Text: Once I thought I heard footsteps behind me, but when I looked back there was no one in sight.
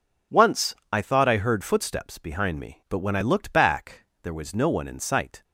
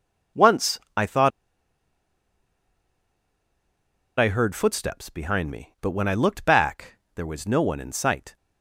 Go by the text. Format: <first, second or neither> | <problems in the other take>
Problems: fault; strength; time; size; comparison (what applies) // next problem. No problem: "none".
first | pauses between "Once" and "I"; slight; at 0.7 s; 0.18 s long; slight in the first // pauses between "thought" and "I"; strong; at 1.3 s; 2.8 s long // pauses between "back" and "there"; slight; at 6.9 s; 0.22 s long; slight in the first